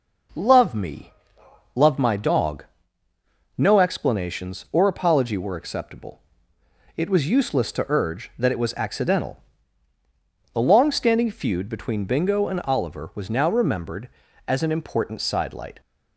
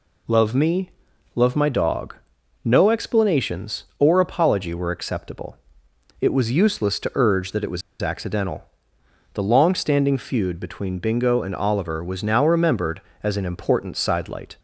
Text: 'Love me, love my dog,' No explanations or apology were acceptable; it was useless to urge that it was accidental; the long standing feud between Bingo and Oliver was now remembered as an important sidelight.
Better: first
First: none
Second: pauses between "was" and "accidental"; slight; at 7.8 s; 0.19 s long

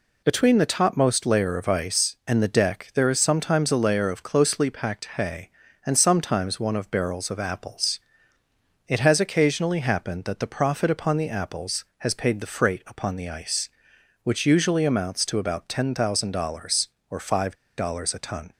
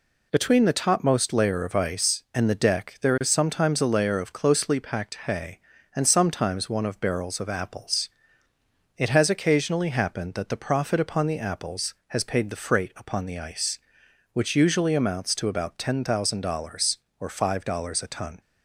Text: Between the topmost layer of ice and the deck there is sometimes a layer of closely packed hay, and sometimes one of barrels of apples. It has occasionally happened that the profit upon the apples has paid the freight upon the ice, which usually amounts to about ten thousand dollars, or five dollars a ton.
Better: second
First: pauses between "five" and "dollars"; slight; at 17.5 s; 0.22 s long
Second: none

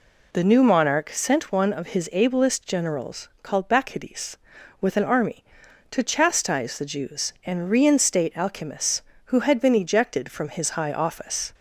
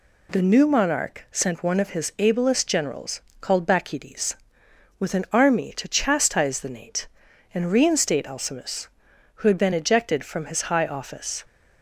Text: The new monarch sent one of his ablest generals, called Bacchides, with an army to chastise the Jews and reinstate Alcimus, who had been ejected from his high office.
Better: first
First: none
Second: says "Nate" for "Jews"; at 6.6 s

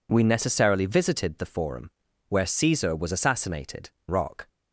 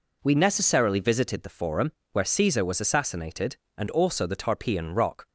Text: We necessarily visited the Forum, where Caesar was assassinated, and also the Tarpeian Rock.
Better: second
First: skips "and also the Tarpeian"; at 4.0 s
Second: none

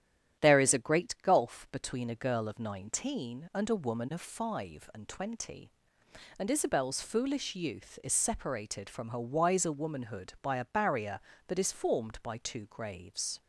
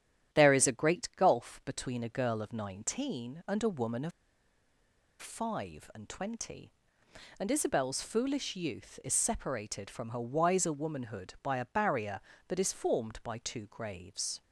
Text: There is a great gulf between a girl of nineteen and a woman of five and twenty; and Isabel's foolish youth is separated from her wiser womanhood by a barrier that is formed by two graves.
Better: first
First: starts louder than the rest; strong; until 1.4 s; 10 dB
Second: starts louder than the rest; strong; until 1.4 s; 10.5 dB // pauses between "of" and "five"; at 4.1 s; 1.1 s long

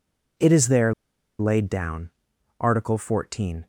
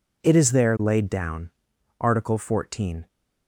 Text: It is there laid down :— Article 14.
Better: second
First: pauses between "there" and "laid"; noticeable; at 0.9 s; 0.46 s long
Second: none

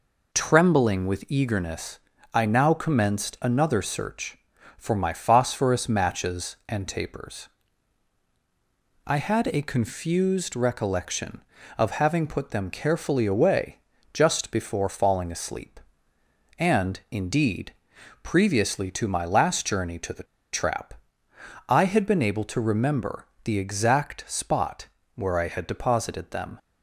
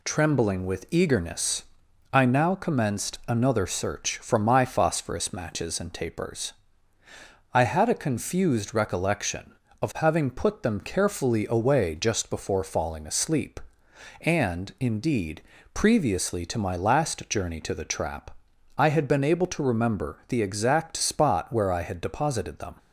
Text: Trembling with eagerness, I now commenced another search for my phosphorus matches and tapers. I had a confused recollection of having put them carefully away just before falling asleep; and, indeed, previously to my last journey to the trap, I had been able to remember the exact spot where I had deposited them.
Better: second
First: pauses between "away" and "just"; slight; at 13.7 s; 0.34 s long // pauses between "the" and "trap"; slight; at 20.2 s; 0.28 s long // pauses between "remember" and "the"; slight; at 23.2 s; 0.18 s long // pauses between "spot" and "where"; slight; at 24.8 s; 0.26 s long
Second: none

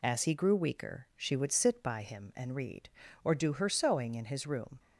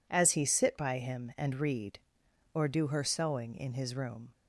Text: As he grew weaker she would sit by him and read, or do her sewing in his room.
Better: first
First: none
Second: skips "grew weaker she would"; at 0.4 s

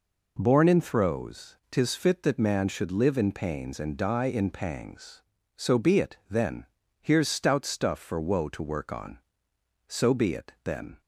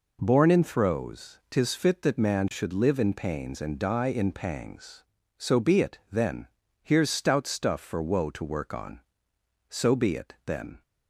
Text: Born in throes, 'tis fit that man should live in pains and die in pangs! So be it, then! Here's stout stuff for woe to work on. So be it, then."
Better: neither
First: none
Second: none

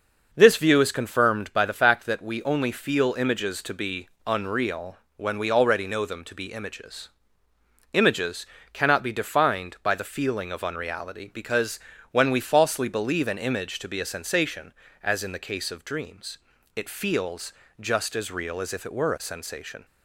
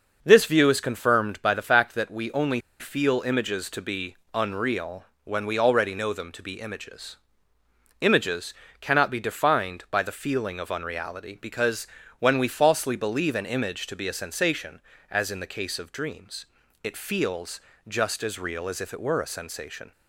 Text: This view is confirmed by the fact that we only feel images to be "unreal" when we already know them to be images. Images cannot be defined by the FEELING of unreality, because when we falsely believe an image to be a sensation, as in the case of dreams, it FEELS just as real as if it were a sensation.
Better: first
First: pauses between "be" and "unreal"; slight; at 4.0 s; 0.18 s long // pauses between "unreal" and "when"; slight; at 4.9 s; 0.22 s long // pauses between "Images" and "cannot"; slight; at 8.4 s; 0.26 s long // pauses between "because" and "when"; slight; at 11.7 s; 0.32 s long // pauses between "FEELS" and "just"; slight; at 17.5 s; 0.26 s long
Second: pauses between "only" and "feel"; slight; at 2.6 s; 0.19 s long // pauses between "be" and "unreal"; slight; at 4.1 s; 0.18 s long // pauses between "unreal" and "when"; slight; at 5.0 s; 0.22 s long // pauses between "Images" and "cannot"; slight; at 8.5 s; 0.26 s long // pauses between "because" and "when"; slight; at 11.8 s; 0.32 s long // pauses between "FEELS" and "just"; slight; at 17.5 s; 0.26 s long

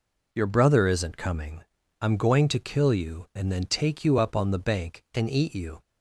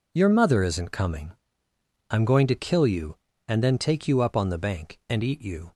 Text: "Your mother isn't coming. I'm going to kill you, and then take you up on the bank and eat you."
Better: second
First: says "brother" for "mother"; at 0.4 s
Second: none

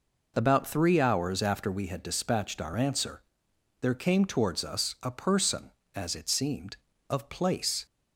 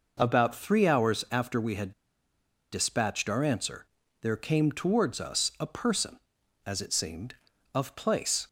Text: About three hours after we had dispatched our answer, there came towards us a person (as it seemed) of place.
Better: first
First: none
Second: pauses between "had" and "dispatched"; noticeable; at 1.9 s; 0.79 s long

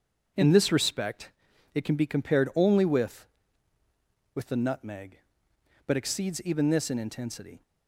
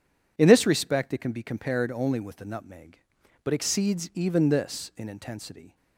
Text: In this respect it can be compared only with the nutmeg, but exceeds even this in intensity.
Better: second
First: starts louder than the rest; until 1.8 s; 7 dB // pauses between "respect" and "it"; at 1.2 s; 0.44 s long // says "with" twice; at 4.3 s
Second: none

